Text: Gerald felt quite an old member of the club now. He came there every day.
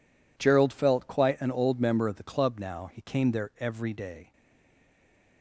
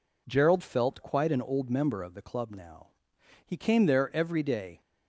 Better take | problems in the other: second | stays silent after the last word; from 4.3 s on; 1.1 s long

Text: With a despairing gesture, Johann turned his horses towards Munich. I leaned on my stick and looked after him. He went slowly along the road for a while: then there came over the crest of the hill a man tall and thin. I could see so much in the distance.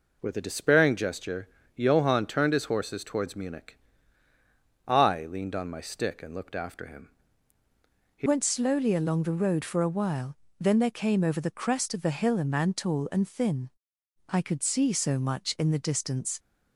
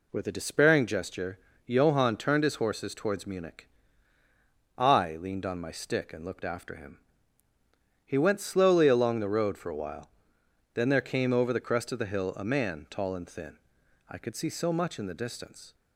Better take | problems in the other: second | changes voice at "went"; from 8.2 s on; 8.1 s long

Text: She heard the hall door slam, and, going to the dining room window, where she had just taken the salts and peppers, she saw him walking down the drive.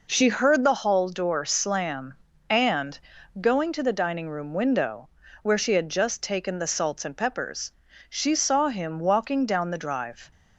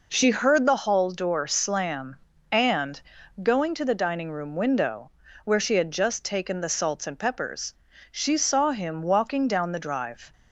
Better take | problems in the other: neither | none

